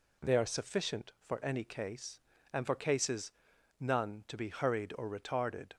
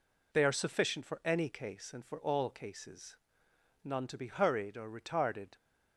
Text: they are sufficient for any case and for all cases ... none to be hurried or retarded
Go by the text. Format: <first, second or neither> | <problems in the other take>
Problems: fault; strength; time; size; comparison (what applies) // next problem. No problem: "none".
second | skips "all"; at 2.7 s